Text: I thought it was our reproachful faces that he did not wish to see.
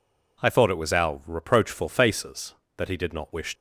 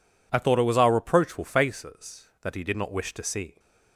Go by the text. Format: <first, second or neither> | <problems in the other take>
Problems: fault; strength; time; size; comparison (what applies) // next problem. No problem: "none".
second | stops before "to see"; at 3.5 s